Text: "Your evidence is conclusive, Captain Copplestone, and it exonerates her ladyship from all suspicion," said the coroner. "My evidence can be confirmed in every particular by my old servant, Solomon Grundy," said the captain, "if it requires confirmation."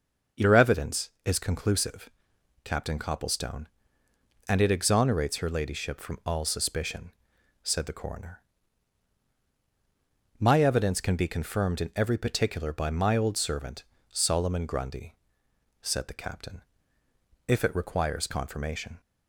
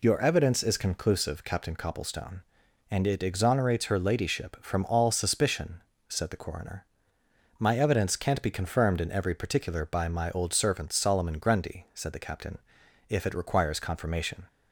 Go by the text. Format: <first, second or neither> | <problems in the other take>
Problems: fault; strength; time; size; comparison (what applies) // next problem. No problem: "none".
first | says "can't" for "can"; at 8.1 s